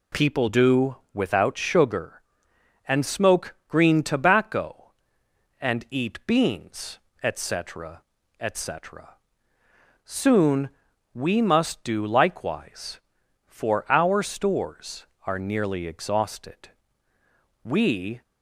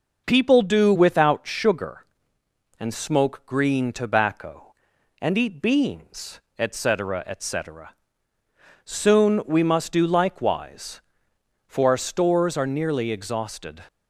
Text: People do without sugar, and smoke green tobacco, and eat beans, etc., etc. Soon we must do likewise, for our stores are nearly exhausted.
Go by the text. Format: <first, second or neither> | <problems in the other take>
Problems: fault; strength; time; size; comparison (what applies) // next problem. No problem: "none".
second | pauses between "do" and "without"; slight; at 0.9 s; 0.16 s long // pauses between "Soon" and "we"; at 10.6 s; 0.44 s long // goes on to say "We"; from 17.6 s on; 0.58 s long